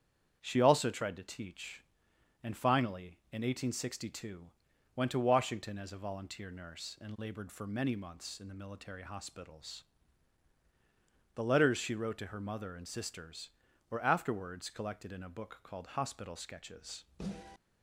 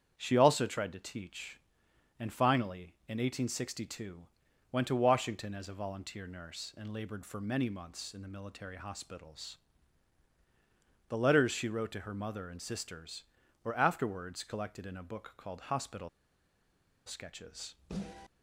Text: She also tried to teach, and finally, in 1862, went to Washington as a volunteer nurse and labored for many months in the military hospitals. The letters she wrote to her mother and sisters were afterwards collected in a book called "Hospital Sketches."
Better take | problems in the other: first | starts louder than the rest; strong; until 1.1 s; 8 dB; strong in the first // pauses between "Hospital" and "Sketches"; at 16.0 s; 0.98 s long

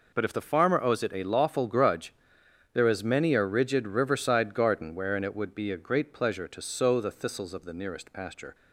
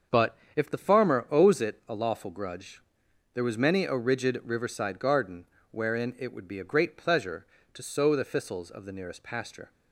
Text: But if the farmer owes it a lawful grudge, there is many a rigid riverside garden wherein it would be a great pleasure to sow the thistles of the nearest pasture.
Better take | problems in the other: first | starts louder than the rest; until 1.2 s; 6.5 dB // pauses between "But" and "if"; slight; at 0.3 s; 0.18 s long // says "was" for "is"; at 3.4 s // pauses between "garden" and "wherein"; slight; at 5.4 s; 0.26 s long

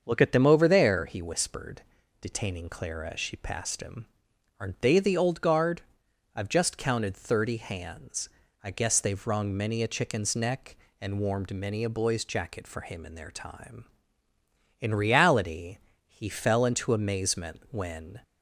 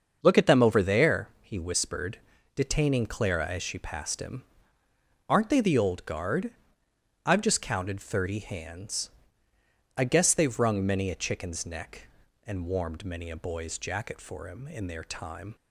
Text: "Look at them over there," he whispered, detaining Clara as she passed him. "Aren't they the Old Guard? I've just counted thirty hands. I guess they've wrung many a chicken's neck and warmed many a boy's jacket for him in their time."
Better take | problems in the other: second | starts louder than the rest; until 1.0 s; 7 dB; also in the second // goes on to say "In reality he fell into amazement when"; strong; from 14.8 s on; 3.4 s long

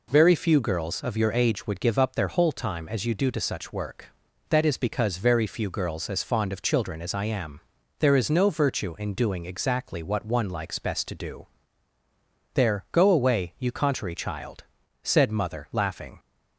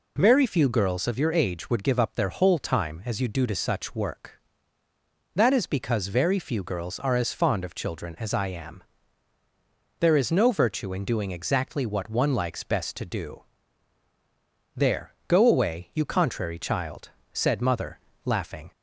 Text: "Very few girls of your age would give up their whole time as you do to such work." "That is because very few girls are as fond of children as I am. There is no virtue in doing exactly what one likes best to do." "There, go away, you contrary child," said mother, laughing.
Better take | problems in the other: second | skips "are"; at 6.0 s

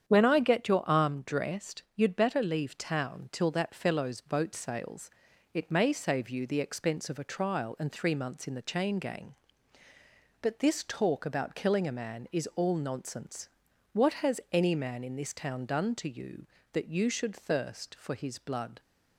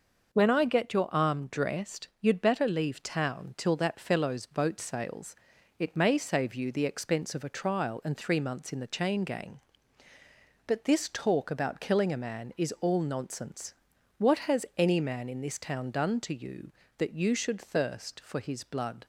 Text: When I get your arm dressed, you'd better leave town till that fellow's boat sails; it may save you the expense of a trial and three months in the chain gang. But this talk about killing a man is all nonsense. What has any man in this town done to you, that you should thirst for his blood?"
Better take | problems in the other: second | starts louder than the rest; strong; until 1.2 s; 8.5 dB

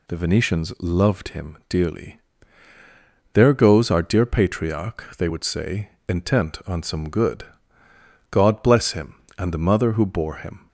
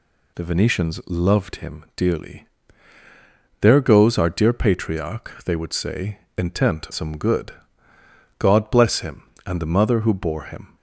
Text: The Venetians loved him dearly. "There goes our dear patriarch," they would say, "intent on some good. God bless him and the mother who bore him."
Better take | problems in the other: first | skips "on"; at 6.8 s

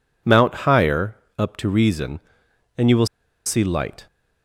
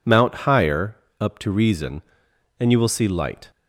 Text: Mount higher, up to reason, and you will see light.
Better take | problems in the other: second | pauses between "will" and "see"; at 3.0 s; 0.39 s long

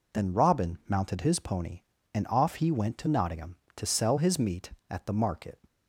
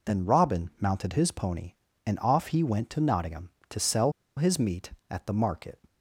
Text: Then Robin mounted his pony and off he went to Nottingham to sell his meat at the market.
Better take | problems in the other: first | pauses between "sell" and "his"; slight; at 4.1 s; 0.24 s long

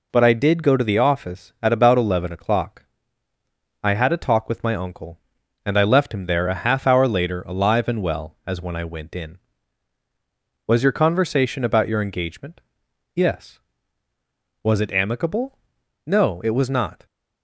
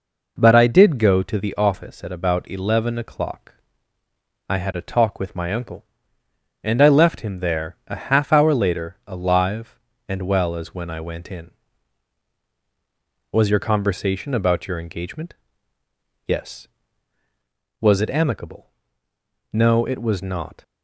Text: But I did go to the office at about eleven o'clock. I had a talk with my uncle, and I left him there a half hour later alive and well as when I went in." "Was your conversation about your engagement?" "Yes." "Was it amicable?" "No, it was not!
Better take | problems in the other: neither | none

